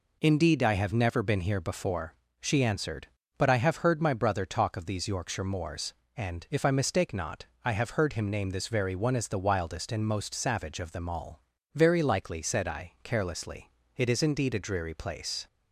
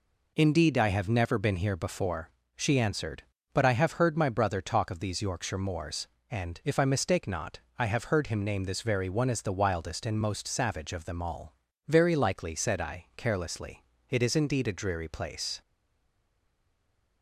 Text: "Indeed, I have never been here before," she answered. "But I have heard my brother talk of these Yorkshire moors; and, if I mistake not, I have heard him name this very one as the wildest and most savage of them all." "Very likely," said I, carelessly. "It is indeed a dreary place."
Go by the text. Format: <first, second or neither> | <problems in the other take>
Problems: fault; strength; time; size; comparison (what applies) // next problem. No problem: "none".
first | stays silent after the last word; noticeable; from 15.6 s on; 1.6 s long